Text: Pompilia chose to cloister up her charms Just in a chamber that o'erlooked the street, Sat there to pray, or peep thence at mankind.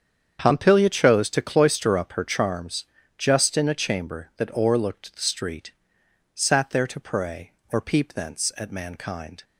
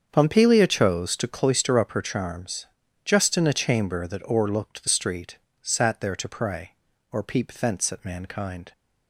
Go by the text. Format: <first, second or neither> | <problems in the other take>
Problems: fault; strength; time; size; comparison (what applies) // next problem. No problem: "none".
neither | starts louder than the rest; strong; the same in both // pauses between "charms" and "Just"; the same in both